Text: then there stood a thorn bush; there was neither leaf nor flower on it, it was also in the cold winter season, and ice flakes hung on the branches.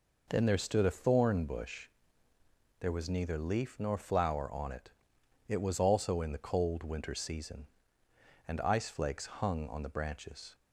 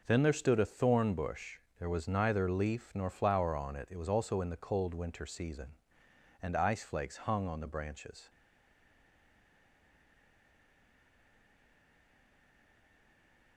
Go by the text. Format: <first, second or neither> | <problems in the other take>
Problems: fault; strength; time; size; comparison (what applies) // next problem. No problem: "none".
first | stays silent after the last word; strong; from 8.2 s on; 5.3 s long